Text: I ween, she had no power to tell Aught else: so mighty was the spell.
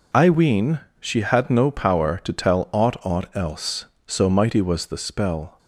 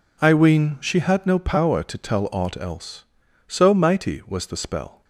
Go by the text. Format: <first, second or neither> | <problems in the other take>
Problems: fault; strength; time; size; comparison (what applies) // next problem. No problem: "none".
second | says "Aught" twice; at 3.0 s